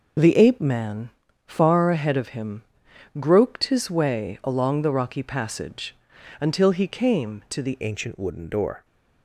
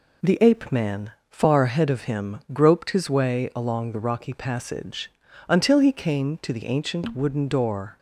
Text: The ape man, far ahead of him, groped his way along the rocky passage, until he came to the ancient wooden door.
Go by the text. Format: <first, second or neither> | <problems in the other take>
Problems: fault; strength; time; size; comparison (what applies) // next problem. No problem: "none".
second | changes voice at "ancient"; from 7.8 s on; 1.0 s long